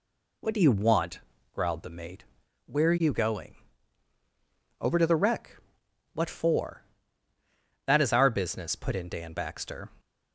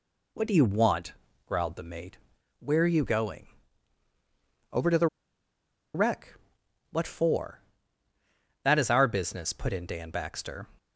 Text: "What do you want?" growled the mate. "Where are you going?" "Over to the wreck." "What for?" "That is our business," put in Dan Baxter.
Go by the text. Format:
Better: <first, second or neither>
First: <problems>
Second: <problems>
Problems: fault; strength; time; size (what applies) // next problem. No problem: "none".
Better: first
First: none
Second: pauses between "the" and "wreck"; noticeable; at 5.0 s; 0.88 s long